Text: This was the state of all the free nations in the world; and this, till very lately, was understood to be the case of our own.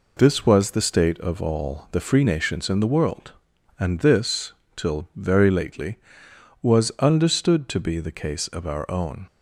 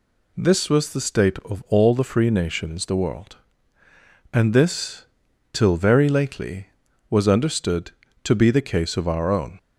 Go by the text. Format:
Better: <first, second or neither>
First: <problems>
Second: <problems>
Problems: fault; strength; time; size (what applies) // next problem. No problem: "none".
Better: first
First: none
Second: skips "in"; at 2.8 s